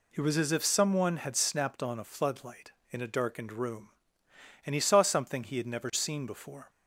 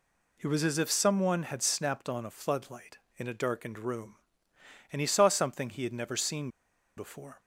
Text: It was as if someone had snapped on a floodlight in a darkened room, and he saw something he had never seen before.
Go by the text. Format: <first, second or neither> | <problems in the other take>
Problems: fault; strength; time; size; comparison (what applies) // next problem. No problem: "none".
first | pauses between "seen" and "before"; noticeable; at 6.4 s; 0.47 s long